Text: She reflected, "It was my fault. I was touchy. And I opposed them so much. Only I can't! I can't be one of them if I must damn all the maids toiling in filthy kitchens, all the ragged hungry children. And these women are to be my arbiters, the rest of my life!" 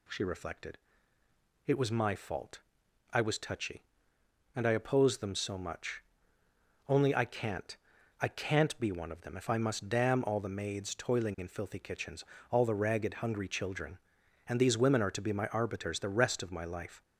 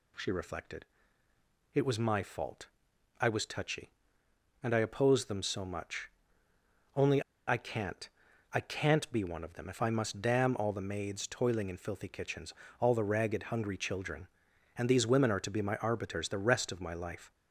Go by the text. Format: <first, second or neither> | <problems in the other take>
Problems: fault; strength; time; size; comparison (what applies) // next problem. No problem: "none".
first | pauses between "Only" and "I"; slight; at 7.2 s; 0.26 s long